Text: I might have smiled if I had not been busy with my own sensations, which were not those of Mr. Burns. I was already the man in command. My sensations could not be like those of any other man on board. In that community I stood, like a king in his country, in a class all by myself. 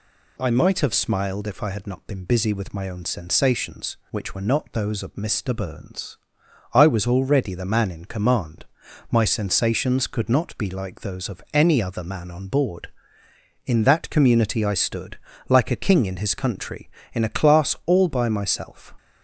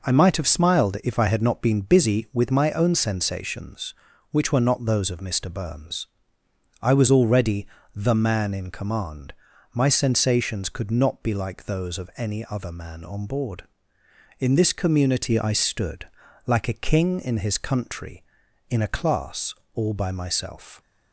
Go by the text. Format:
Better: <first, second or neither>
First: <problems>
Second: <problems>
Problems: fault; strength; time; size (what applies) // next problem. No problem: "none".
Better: first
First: none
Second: pauses between "already" and "the"; slight; at 7.6 s; 0.26 s long // says "this" for "that"; at 14.5 s // pauses between "class" and "all"; slight; at 19.5 s; 0.22 s long